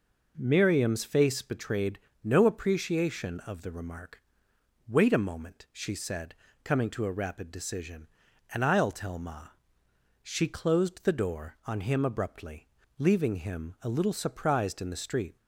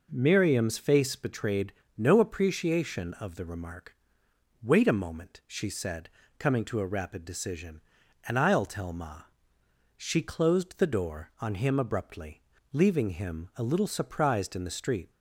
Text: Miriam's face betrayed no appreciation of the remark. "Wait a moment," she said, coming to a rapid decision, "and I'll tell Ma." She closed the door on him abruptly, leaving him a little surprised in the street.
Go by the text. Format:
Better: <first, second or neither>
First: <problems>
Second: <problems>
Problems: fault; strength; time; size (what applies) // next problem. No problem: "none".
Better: neither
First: pauses between "betrayed" and "no"; slight; at 1.9 s; 0.24 s long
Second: pauses between "betrayed" and "no"; slight; at 1.7 s; 0.24 s long